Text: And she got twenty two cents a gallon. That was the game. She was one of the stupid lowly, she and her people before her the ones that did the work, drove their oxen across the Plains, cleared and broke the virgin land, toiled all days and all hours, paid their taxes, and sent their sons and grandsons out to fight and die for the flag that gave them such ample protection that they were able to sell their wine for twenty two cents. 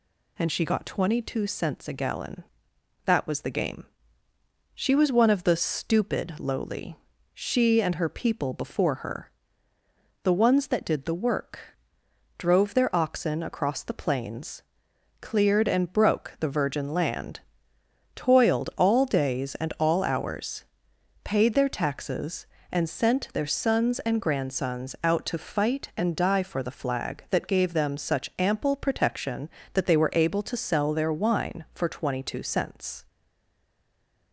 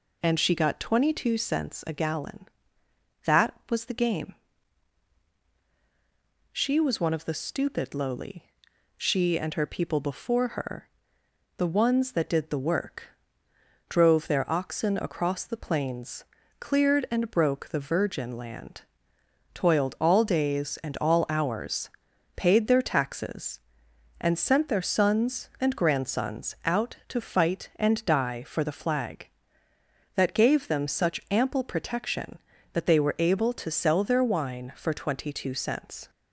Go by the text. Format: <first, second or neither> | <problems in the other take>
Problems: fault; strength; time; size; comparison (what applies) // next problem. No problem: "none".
second | pauses between "her" and "the"; noticeable; at 9.2 s; 0.92 s long; noticeable in the second // stays silent after the last word; noticeable; from 33.0 s on; 1.3 s long